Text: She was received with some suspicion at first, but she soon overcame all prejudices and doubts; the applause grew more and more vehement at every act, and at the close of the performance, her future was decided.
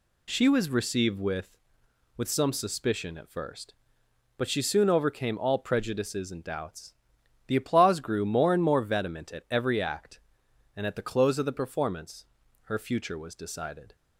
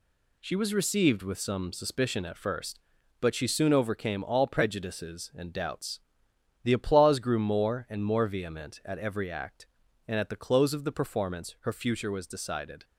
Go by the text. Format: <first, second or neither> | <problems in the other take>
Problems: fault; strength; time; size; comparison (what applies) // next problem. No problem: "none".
second | says "with" twice; at 2.1 s